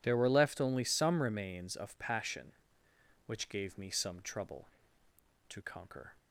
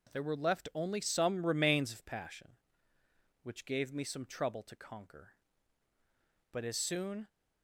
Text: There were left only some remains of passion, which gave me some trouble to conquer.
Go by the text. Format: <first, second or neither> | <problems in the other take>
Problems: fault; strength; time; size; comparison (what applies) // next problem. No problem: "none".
first | goes on to say "But as soon"; noticeable; from 6.5 s on; 0.76 s long